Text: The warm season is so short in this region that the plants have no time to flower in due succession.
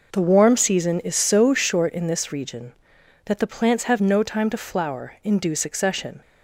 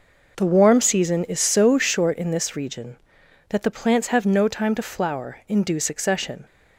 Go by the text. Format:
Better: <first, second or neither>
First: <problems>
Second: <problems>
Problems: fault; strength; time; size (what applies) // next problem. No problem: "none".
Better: neither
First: none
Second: none